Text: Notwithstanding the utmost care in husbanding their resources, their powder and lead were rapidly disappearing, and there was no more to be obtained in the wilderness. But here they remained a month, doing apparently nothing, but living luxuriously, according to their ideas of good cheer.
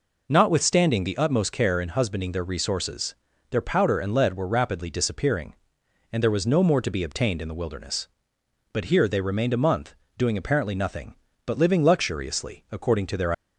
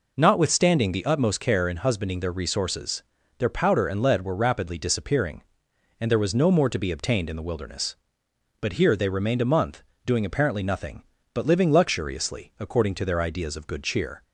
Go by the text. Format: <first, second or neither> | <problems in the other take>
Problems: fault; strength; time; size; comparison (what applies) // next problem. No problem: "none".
second | stops before "ideas of good cheer"; at 13.3 s